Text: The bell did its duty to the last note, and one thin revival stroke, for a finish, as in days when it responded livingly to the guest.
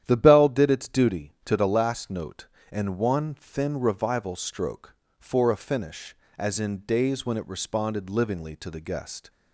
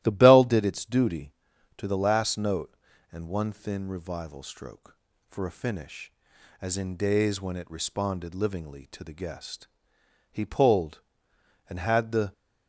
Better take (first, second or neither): first